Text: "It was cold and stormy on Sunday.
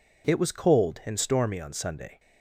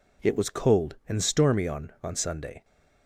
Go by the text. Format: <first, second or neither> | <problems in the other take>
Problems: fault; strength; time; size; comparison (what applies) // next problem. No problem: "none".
first | says "on" twice; at 2.0 s